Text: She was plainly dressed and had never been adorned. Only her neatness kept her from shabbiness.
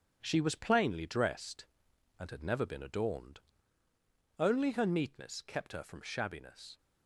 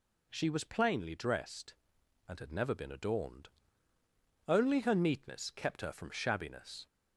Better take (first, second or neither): second